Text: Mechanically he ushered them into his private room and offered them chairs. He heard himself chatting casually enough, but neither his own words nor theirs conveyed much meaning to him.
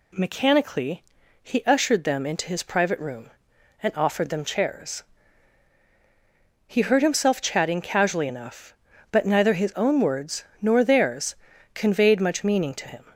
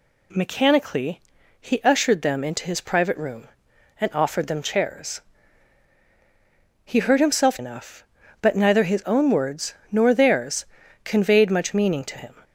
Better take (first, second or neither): first